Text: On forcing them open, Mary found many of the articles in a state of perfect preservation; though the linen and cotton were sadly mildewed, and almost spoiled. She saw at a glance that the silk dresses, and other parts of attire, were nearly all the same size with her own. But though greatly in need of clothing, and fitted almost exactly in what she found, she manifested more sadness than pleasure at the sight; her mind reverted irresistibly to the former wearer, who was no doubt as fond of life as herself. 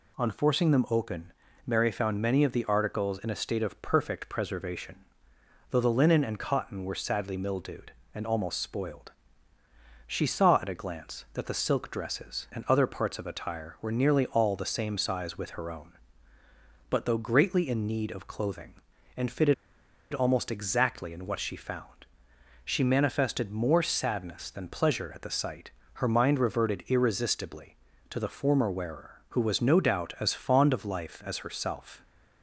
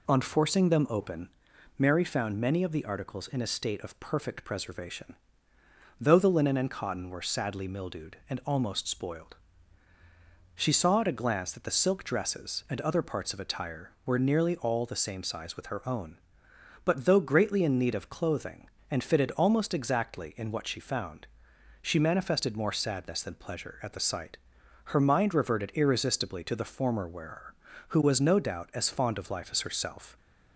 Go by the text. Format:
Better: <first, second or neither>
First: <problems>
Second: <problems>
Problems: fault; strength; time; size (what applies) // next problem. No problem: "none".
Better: second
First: pauses between "fitted" and "almost"; noticeable; at 19.5 s; 0.59 s long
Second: none